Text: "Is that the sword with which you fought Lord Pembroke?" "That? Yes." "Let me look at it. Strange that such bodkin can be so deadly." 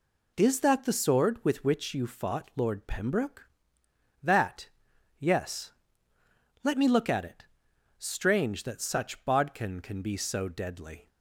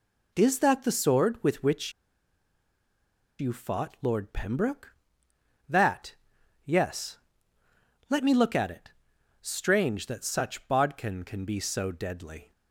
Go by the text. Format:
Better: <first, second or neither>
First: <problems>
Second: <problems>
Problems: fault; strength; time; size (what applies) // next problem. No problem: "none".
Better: first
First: none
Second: pauses between "which" and "you"; strong; at 1.9 s; 1.4 s long